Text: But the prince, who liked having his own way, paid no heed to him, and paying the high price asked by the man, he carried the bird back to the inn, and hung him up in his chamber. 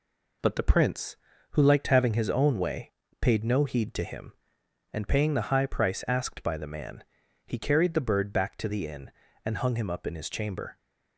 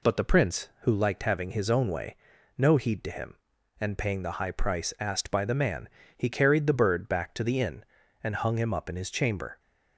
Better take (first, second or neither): first